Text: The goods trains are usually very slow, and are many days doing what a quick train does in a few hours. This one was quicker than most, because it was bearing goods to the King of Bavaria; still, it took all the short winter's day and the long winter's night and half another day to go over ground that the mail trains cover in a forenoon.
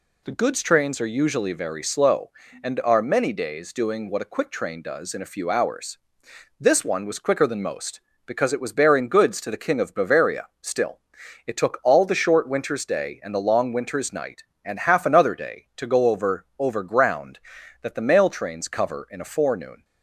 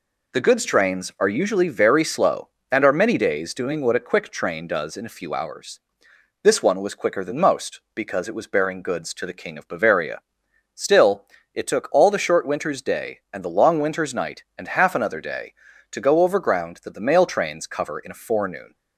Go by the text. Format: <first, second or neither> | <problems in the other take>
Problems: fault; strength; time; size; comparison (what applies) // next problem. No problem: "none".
second | says "over" twice; at 16.5 s